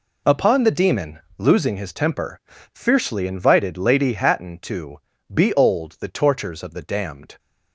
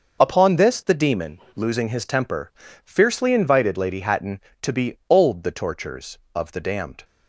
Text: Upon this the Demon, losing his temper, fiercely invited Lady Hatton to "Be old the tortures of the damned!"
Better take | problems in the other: second | skips "this"; at 0.6 s // pauses between "to" and "Be"; slight; at 4.9 s; 0.34 s long

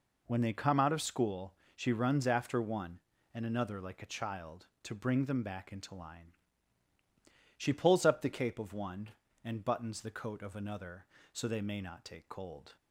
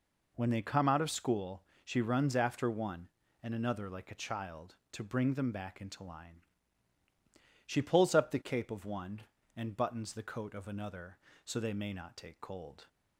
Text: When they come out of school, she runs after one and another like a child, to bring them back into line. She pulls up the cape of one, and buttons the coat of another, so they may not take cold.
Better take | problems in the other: neither | none

